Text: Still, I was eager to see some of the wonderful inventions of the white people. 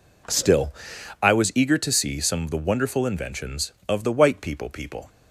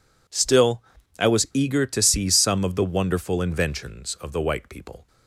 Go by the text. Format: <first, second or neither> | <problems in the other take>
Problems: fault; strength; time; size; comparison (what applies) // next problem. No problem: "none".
second | says "people" twice; at 4.6 s